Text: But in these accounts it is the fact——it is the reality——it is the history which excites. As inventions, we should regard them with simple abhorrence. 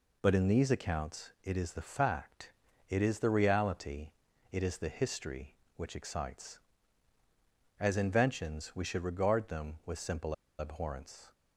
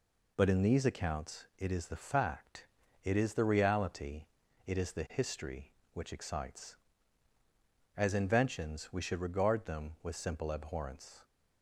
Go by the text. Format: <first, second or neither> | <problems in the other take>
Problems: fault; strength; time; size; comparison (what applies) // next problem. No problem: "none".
second | pauses between "simple" and "abhorrence"; slight; at 10.3 s; 0.25 s long